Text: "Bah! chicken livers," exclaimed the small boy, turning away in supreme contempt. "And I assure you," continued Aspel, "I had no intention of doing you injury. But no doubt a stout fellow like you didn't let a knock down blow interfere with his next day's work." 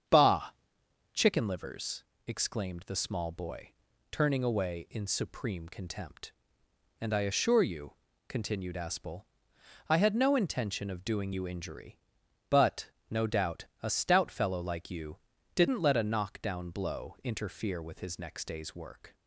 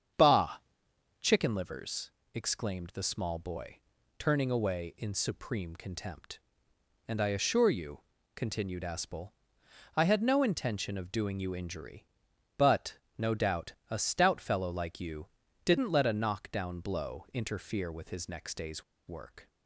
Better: first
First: starts louder than the rest; strong; until 1.7 s; 8 dB // pauses between "But" and "no"; slight; at 12.9 s; 0.18 s long // pauses between "doubt" and "a"; slight; at 13.6 s; 0.16 s long // pauses between "you" and "didn't"; at 15.1 s; 0.38 s long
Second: starts louder than the rest; strong; until 1.7 s; 8 dB // pauses between "But" and "no"; slight; at 12.9 s; 0.18 s long // pauses between "doubt" and "a"; slight; at 13.7 s; 0.16 s long // pauses between "you" and "didn't"; at 15.2 s; 0.38 s long // pauses between "day's" and "work"; slight; at 18.8 s; 0.25 s long

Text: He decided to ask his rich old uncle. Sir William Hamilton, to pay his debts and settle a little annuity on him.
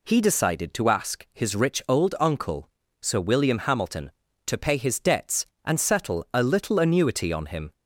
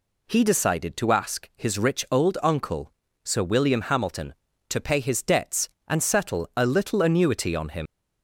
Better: first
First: none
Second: leaves "him" unfinished; at 7.8 s; 95 ms

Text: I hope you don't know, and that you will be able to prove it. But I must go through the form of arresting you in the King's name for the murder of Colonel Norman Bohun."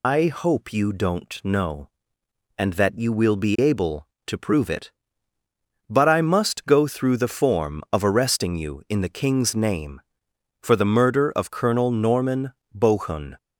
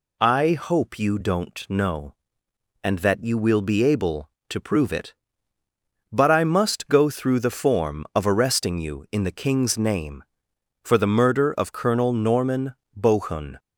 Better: second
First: loses the start of "I"; at 0.0 s; 105 ms // pauses between "Norman" and "Bohun"; slight; at 12.5 s; 0.20 s long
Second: pauses between "Norman" and "Bohun"; slight; at 12.7 s; 0.20 s long

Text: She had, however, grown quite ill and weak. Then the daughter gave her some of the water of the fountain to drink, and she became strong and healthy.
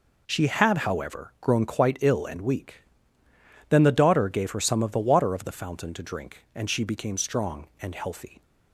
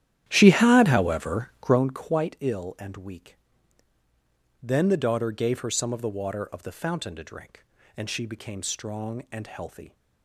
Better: first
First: none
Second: starts louder than the rest; strong; until 1.8 s; 11.5 dB

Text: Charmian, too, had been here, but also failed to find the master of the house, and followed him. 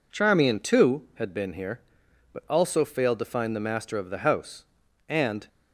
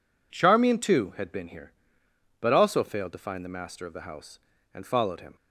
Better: second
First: stops before "followed him"; at 5.4 s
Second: none

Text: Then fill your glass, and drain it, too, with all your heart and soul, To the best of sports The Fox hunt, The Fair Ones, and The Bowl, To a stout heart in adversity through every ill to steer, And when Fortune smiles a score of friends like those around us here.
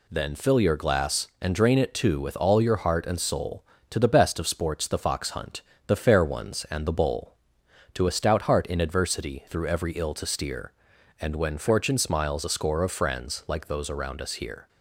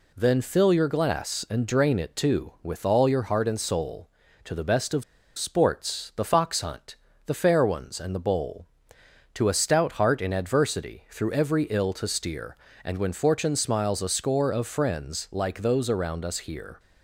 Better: first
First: none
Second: pauses between "of" and "sports"; slight; at 5.0 s; 0.35 s long

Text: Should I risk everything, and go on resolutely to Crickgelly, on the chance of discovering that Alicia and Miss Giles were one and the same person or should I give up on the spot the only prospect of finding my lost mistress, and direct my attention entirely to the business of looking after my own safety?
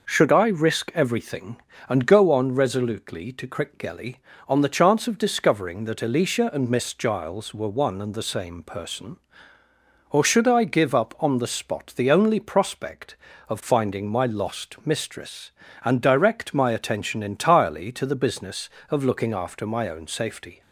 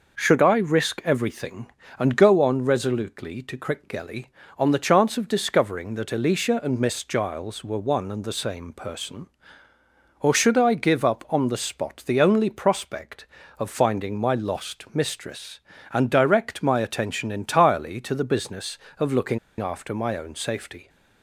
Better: first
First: none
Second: pauses between "looking" and "after"; slight; at 19.3 s; 0.22 s long

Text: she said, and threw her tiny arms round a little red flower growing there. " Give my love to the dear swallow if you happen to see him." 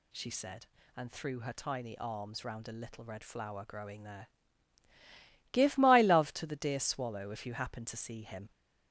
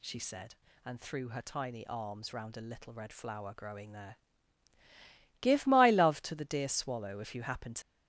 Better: first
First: none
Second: stops before "see him"; at 7.8 s

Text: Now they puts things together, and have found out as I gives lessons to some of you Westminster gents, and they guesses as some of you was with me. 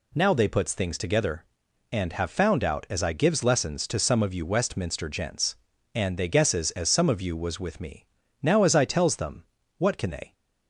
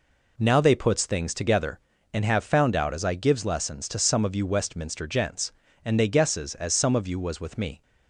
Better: second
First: goes on to say "Now as I tells them what can they"; strong; from 8.4 s on; 1.9 s long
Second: none

